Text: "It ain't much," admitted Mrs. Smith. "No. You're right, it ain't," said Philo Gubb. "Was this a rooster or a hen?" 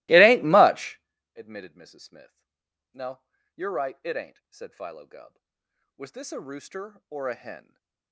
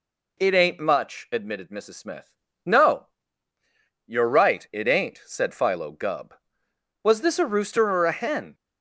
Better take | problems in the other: second | starts louder than the rest; strong; until 1.1 s; 21 dB // stays silent after the last word; slight; from 7.6 s on; 0.5 s long

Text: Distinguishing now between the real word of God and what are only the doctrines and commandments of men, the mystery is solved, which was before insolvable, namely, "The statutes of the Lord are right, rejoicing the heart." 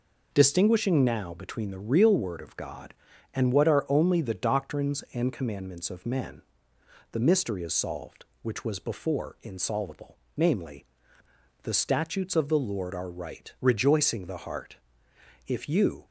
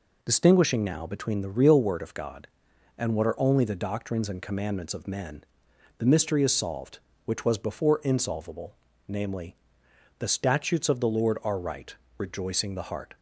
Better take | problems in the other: second | goes on to say "If you"; from 15.4 s on; 0.58 s long

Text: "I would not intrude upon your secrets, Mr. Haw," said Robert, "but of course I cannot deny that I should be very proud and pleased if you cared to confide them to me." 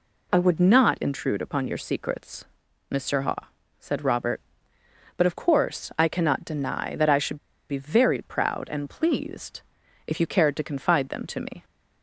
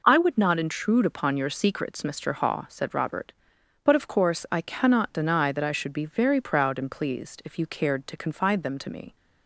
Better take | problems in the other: second | pauses between "should" and "be"; slight; at 7.3 s; 0.32 s long // pauses between "pleased" and "if"; at 9.6 s; 0.44 s long

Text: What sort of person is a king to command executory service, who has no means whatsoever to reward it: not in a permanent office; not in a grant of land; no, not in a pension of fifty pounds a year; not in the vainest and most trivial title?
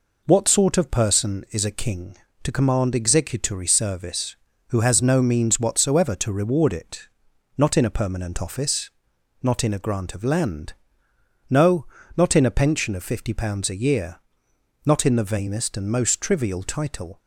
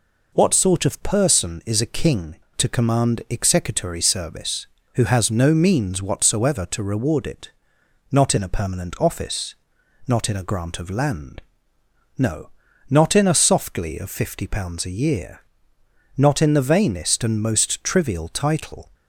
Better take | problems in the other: first | says "softly" for "pension"; at 13.3 s

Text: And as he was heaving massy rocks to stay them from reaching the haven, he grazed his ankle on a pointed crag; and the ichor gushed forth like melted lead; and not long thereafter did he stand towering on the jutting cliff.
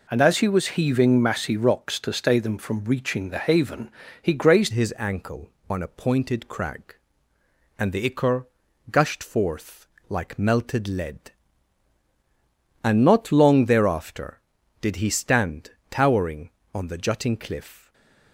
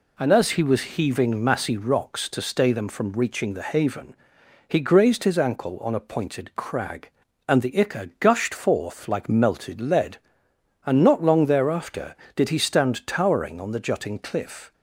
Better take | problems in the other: second | changes voice at "his"; from 4.7 s on; 13.2 s long // pauses between "ichor" and "gushed"; at 8.4 s; 0.44 s long // pauses between "forth" and "like"; slight; at 9.8 s; 0.22 s long // pauses between "stand" and "towering"; slight; at 15.7 s; 0.18 s long // stays silent after the last word; slight; from 17.7 s on; 0.6 s long

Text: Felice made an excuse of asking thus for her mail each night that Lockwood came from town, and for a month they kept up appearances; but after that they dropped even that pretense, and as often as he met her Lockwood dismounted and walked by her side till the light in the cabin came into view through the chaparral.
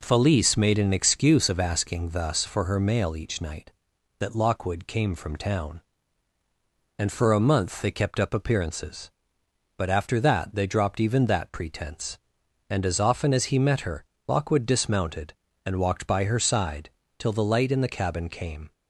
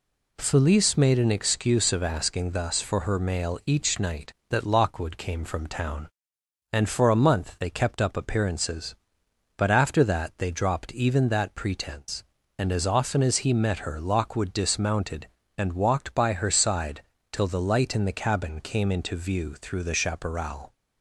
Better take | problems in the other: second | pauses between "her" and "Lockwood"; slight; at 14.0 s; 0.22 s long // pauses between "side" and "till"; slight; at 16.8 s; 0.30 s long; slight in the second // stops before "into view through the chaparral"; at 18.7 s

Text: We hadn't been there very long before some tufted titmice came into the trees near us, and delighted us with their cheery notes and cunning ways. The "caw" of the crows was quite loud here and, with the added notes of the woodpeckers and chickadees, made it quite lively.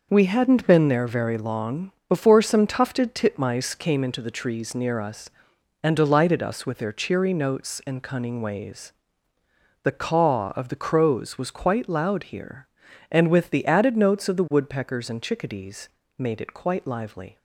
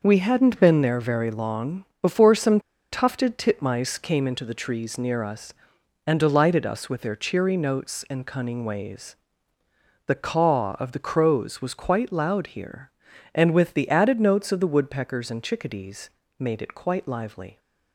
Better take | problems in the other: first | pauses between "long" and "before"; slight; at 1.8 s; 0.16 s long; slight in the first // pauses between "some" and "tufted"; slight; at 2.5 s; 0.33 s long

